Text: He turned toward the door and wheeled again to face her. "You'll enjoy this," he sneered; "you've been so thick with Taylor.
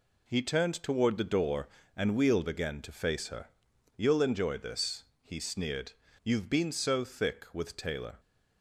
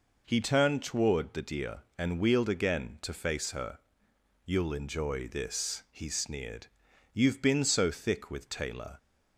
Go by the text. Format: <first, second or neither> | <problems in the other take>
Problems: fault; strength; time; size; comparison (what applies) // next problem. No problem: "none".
first | says "deer" for "door"; at 1.4 s